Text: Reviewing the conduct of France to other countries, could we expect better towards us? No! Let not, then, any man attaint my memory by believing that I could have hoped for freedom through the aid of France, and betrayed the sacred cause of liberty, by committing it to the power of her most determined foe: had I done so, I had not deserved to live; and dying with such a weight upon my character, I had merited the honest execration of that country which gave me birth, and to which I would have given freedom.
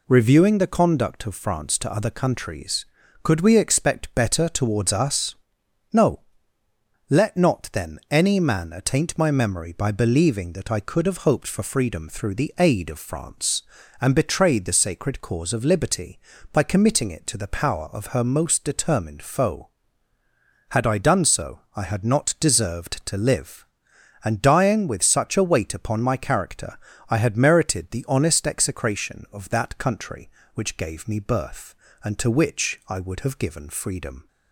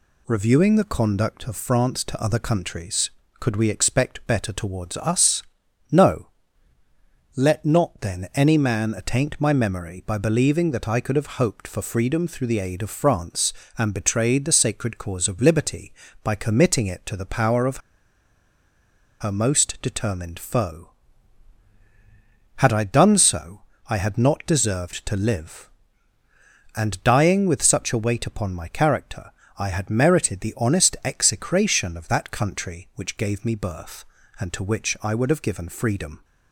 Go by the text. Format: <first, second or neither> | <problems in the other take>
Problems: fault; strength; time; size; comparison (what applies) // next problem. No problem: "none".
first | pauses between "of" and "her"; strong; at 17.7 s; 1.4 s long